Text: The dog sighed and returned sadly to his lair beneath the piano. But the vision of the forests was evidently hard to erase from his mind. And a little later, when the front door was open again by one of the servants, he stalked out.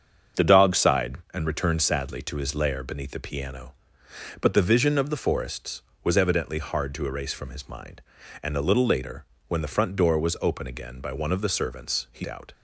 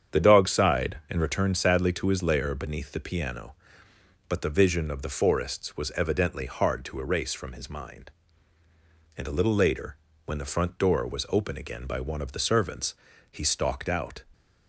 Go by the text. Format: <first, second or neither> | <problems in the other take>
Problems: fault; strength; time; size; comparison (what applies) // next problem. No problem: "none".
second | starts louder than the rest; until 1.5 s; 7 dB; strong in the second // skips "stalked"; at 12.2 s